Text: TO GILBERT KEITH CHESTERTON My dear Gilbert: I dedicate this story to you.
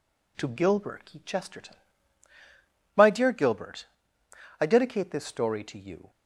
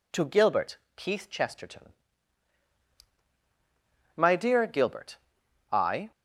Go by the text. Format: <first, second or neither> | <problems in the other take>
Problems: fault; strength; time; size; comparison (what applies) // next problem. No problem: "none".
first | pauses between "GILBERT" and "KEITH"; slight; at 0.7 s; 0.18 s long // pauses between "CHESTERTON" and "My"; strong; at 1.9 s; 2.2 s long; also in the first // stops before "dedicate this story to you"; at 6.1 s